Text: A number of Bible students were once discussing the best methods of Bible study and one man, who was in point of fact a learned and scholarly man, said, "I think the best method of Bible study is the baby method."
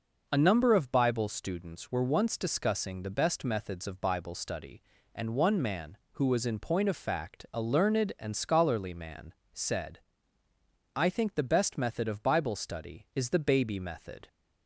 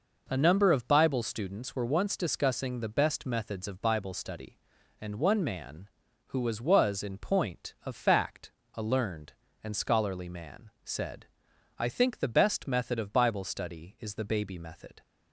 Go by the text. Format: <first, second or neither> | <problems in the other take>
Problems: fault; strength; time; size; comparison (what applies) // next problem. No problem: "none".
first | says "was" twice; at 6.5 s // pauses between "fact" and "a"; slight; at 8.5 s; 0.22 s long